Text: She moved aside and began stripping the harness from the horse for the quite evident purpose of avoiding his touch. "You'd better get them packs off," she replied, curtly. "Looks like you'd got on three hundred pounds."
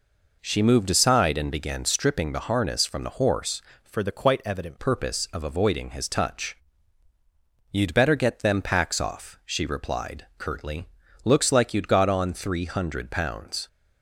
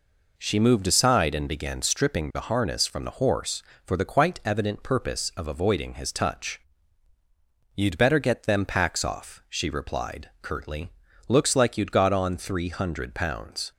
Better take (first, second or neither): second